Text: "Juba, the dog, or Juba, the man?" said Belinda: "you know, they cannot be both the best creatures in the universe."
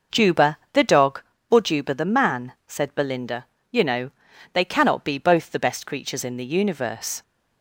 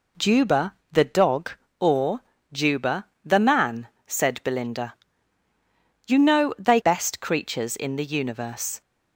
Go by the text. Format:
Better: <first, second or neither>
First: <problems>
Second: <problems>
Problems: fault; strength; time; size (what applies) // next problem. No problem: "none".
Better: first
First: none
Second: pauses between "or" and "Juba"; slight; at 2.2 s; 0.32 s long // skips "cannot be both the"; at 6.8 s